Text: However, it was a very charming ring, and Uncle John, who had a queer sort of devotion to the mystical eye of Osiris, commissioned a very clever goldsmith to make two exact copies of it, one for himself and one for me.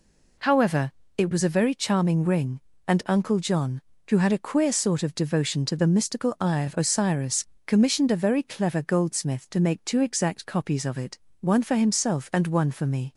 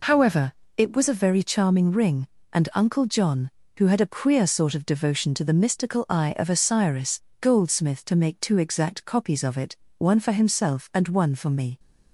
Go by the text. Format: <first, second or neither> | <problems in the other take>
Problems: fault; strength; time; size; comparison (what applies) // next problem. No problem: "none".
first | skips "commissioned a very clever"; at 7.3 s